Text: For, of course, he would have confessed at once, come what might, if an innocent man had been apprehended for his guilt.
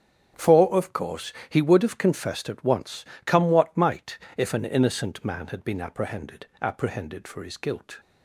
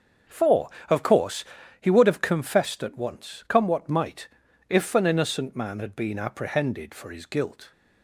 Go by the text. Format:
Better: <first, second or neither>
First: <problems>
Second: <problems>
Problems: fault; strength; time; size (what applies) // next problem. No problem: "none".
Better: second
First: starts louder than the rest; strong; until 1.5 s; 8 dB // says "apprehended" twice; at 6.6 s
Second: starts louder than the rest; until 1.8 s; 6.5 dB